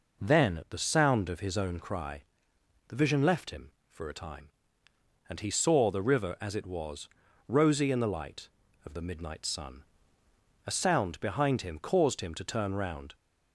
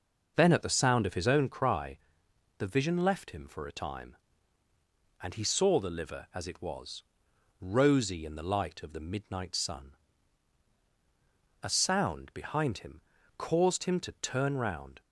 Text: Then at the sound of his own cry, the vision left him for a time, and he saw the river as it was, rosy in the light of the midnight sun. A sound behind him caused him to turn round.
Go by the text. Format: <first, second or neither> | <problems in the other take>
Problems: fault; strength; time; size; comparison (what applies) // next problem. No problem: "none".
first | says "liver" for "river"; at 5.9 s // pauses between "him" and "caused"; slight; at 13.0 s; 0.36 s long